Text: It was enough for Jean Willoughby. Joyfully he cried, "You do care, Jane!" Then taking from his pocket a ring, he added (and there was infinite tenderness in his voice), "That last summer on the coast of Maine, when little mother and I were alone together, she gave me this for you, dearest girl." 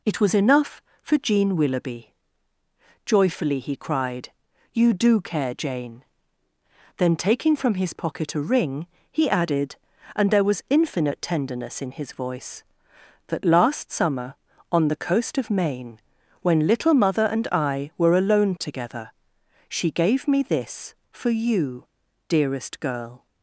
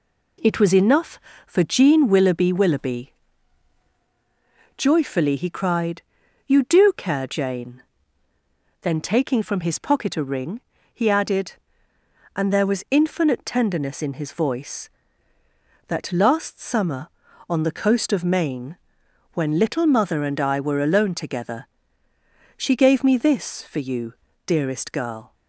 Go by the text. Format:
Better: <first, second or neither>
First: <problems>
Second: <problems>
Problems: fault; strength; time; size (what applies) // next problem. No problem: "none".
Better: first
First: none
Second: says "Willoughby" twice; at 2.5 s